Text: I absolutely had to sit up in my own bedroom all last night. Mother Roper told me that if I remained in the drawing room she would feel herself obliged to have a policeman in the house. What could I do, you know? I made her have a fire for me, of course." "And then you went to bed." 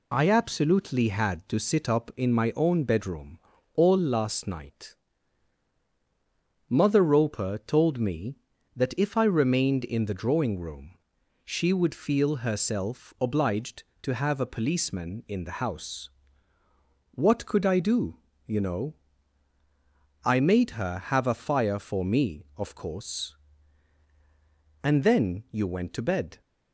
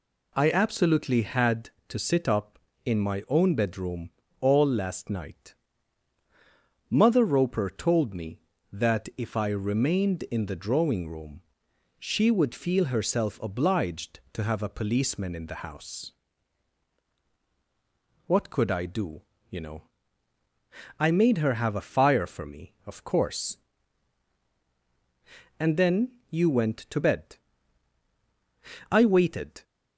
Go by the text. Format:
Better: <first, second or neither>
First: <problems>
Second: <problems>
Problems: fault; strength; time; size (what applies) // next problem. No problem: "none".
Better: first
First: pauses between "bedroom" and "all"; slight; at 3.3 s; 0.36 s long // pauses between "room" and "she"; noticeable; at 10.9 s; 0.50 s long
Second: pauses between "bedroom" and "all"; slight; at 4.1 s; 0.28 s long // pauses between "room" and "she"; noticeable; at 11.4 s; 0.58 s long // pauses between "then" and "you"; slight; at 26.1 s; 0.18 s long // goes on to say "I waited"; noticeable; from 28.8 s on; 0.74 s long